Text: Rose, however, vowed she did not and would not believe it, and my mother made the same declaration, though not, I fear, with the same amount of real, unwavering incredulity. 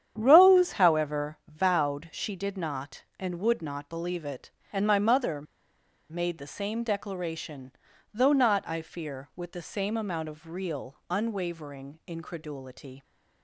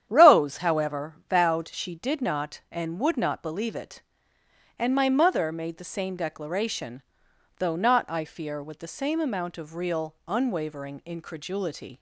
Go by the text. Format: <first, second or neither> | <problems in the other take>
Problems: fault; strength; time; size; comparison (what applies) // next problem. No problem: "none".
second | starts louder than the rest; strong; until 1.1 s; 9 dB; strong in the second // pauses between "mother" and "made"; noticeable; at 5.4 s; 0.67 s long